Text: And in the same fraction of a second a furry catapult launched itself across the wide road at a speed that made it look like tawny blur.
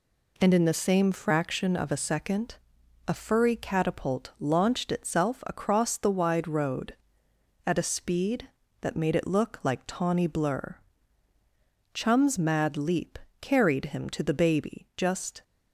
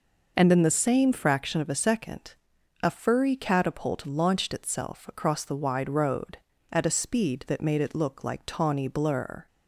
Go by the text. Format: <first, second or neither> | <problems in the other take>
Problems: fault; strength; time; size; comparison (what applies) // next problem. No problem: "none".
second | pauses between "second" and "a"; noticeable; at 2.5 s; 0.52 s long; noticeable in the second // goes on to say "Chum's mad leap carried him to the baby just"; strong; from 11.9 s on; 3.4 s long